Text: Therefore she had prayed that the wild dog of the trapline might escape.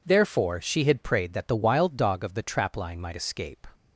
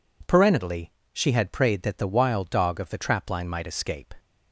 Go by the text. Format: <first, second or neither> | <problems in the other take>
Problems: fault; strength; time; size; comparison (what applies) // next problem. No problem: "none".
first | says "Parentally" for "Therefore"; at 0.2 s